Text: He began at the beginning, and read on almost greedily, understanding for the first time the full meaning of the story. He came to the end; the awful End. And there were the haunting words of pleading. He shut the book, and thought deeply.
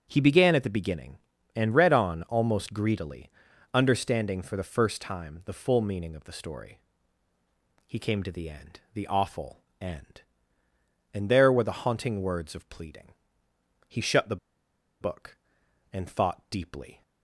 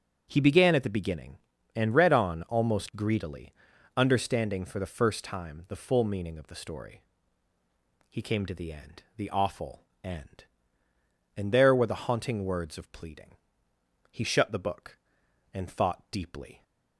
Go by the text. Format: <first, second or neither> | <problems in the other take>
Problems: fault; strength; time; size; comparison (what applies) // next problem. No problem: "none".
second | starts louder than the rest; strong; until 1.1 s; 8 dB; also in the second // pauses between "awful" and "End"; slight; at 9.6 s; 0.20 s long; slight in the second // pauses between "the" and "book"; noticeable; at 14.3 s; 0.64 s long